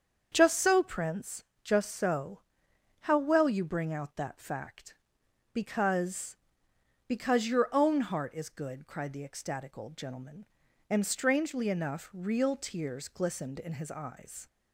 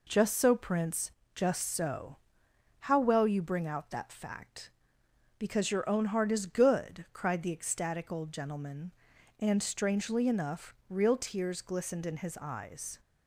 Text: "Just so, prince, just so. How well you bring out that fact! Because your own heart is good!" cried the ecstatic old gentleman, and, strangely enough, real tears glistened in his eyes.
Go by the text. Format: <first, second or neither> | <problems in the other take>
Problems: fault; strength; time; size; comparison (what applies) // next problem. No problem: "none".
second | starts louder than the rest; strong; until 1.3 s; 7 dB // says "Because" twice; at 7.0 s